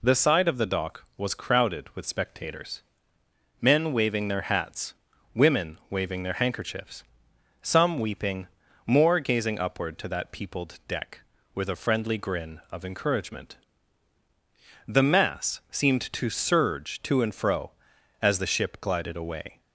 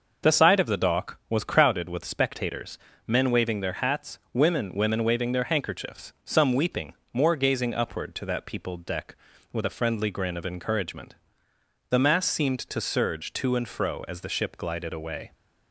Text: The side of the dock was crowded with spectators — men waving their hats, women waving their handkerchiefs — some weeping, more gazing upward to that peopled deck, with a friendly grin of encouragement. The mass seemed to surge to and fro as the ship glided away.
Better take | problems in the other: first | says "women" twice; at 4.7 s

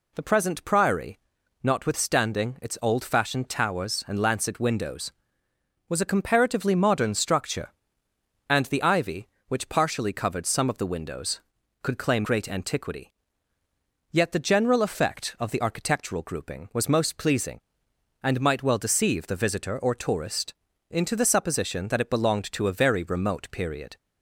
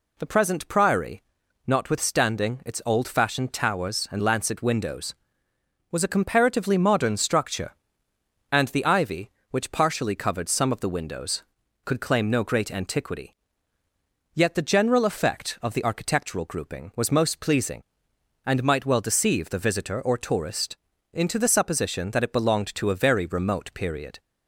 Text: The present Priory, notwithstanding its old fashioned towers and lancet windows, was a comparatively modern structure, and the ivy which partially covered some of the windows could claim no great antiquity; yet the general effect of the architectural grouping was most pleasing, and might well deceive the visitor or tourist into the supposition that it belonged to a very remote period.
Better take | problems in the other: second | skips "no"; at 12.2 s // pauses between "tourist" and "into"; slight; at 20.5 s; 0.36 s long; slight in the second

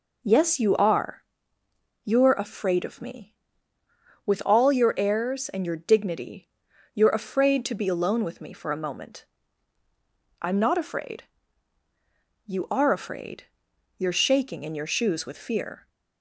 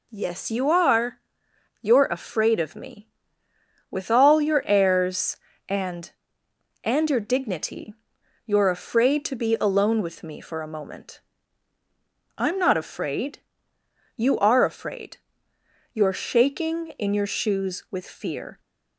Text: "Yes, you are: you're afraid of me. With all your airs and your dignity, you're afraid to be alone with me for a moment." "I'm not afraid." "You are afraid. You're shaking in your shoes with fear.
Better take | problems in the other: first | says "and" twice; at 6.8 s

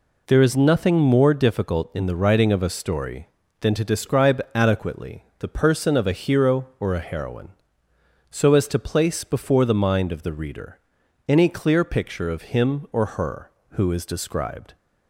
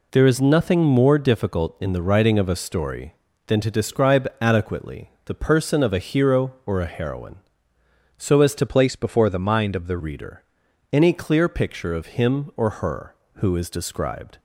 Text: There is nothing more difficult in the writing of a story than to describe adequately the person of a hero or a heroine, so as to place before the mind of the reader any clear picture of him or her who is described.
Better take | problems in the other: first | pauses between "adequately" and "the"; slight; at 5.0 s; 0.18 s long; slight in the first // changes voice from "place" to "the"; from 8.6 to 9.9 s; 1.3 s long // pauses between "reader" and "any"; noticeable; at 10.4 s; 0.48 s long; noticeable in the first

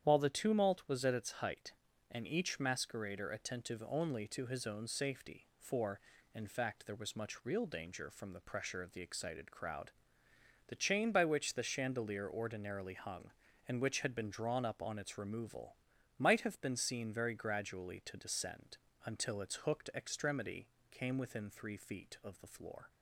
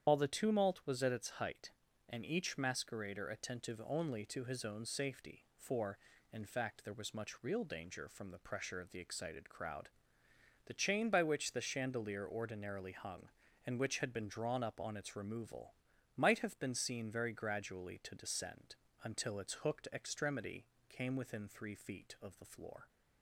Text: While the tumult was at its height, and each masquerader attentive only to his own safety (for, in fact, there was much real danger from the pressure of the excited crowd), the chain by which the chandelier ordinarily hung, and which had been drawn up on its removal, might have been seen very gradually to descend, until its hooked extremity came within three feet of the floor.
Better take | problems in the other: first | loses the start of "While"; at 0.0 s; 50 ms // starts louder than the rest; strong; until 1.1 s; 9.5 dB; strong in the first // pauses between "extremity" and "came"; slight; at 20.6 s; 0.22 s long; slight in the first

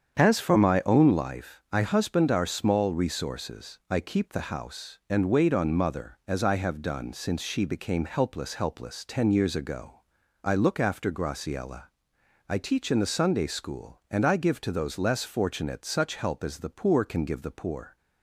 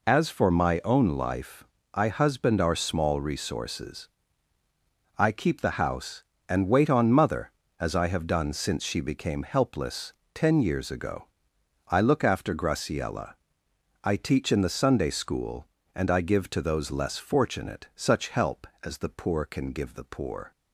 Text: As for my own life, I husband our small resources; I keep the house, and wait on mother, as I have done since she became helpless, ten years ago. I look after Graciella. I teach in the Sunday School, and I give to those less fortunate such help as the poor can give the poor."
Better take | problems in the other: second | starts louder than the rest; strong; until 1.2 s; 8 dB // says "helpless" twice; at 8.5 s

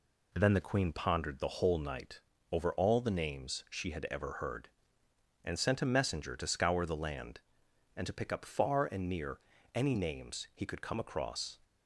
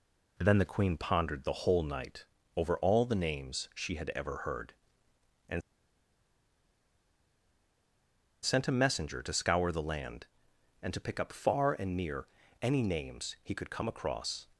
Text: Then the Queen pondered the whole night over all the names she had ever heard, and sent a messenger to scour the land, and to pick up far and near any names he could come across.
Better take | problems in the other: first | pauses between "night" and "over"; slight; at 2.2 s; 0.30 s long; slight in the first // pauses between "and" and "sent"; strong; at 5.6 s; 2.8 s long // pauses between "near" and "any"; slight; at 12.2 s; 0.34 s long; slight in the first

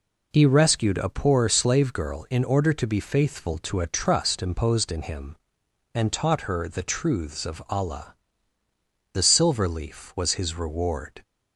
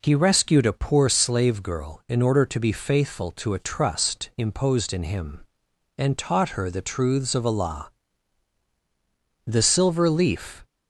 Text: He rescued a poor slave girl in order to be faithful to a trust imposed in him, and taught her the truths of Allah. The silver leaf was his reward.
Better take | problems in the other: first | stops before "was his reward"; at 10.6 s

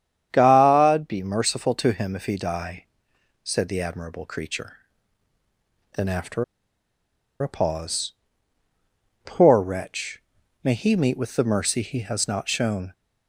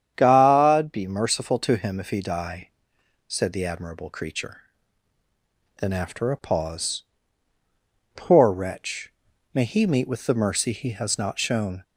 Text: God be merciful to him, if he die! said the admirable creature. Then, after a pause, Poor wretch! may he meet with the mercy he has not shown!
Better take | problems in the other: second | starts louder than the rest; strong; until 1.3 s; 9 dB; strong in the second // pauses between "after" and "a"; noticeable; at 6.4 s; 0.97 s long

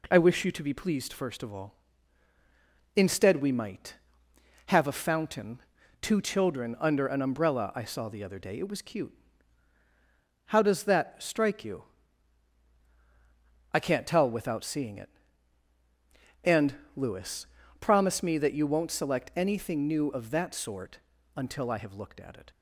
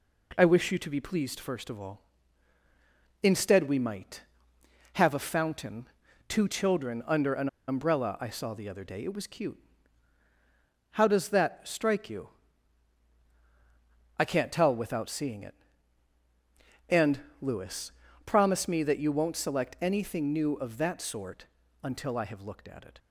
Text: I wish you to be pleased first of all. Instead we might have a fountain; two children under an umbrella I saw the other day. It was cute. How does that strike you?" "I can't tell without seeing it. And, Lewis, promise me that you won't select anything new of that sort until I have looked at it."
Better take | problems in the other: first | pauses between "an" and "umbrella"; slight; at 7.4 s; 0.19 s long // pauses between "sort" and "until"; slight; at 21.4 s; 0.34 s long; slight in the first

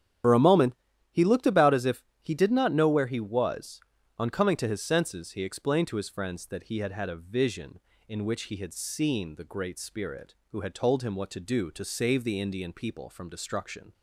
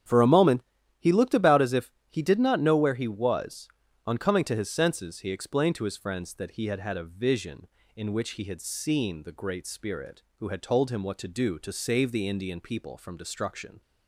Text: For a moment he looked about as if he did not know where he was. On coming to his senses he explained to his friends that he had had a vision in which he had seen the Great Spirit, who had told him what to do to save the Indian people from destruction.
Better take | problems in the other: second | loses the start of "For"; at 0.2 s; 65 ms // starts louder than the rest; strong; until 1.6 s; 10 dB; strong in the second // pauses between "moment" and "he"; at 0.7 s; 0.40 s long; also in the second // pauses between "if" and "he"; slight; at 2.0 s; 0.18 s long; slight in the second

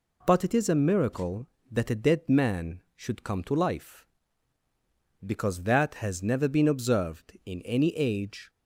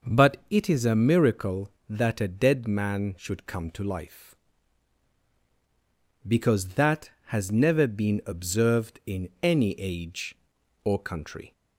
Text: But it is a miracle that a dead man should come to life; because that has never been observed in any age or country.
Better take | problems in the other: second | stops before "or country"; at 8.4 s

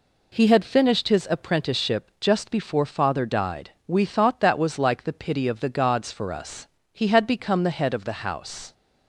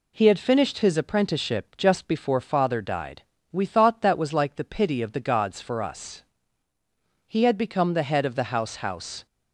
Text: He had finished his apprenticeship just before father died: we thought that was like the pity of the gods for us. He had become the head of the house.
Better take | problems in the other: first | says "house" twice; at 8.7 s

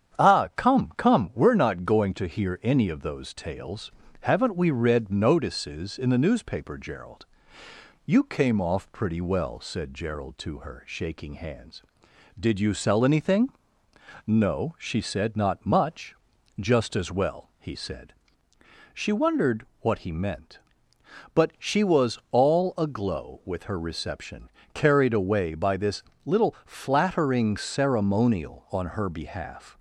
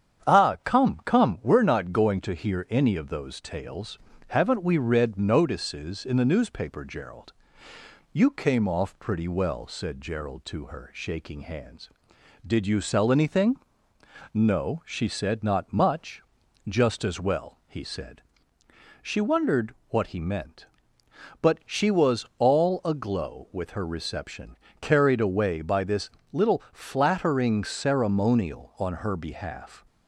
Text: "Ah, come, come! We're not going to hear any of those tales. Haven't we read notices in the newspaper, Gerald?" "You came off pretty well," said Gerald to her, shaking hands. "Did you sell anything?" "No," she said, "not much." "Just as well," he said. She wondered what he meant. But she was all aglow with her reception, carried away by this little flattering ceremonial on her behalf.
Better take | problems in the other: neither | starts louder than the rest; strong; the same in both // pauses between "wondered" and "what"; slight; the same in both // pauses between "this" and "little"; slight; the same in both

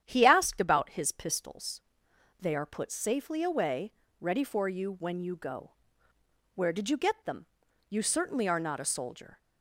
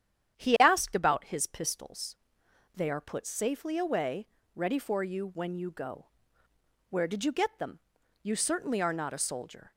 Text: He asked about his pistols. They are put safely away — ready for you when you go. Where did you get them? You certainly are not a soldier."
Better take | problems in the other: neither | starts louder than the rest; strong; the same in both

